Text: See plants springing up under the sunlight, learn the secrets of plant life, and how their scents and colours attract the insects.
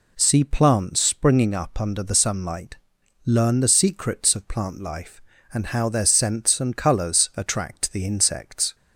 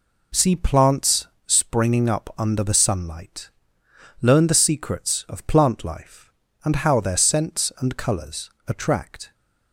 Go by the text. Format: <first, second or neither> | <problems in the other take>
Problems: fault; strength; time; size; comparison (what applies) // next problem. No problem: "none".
first | pauses between "plants" and "springing"; slight; at 1.2 s; 0.18 s long // pauses between "colours" and "attract"; slight; at 8.4 s; 0.18 s long // stops before "the insects"; at 9.3 s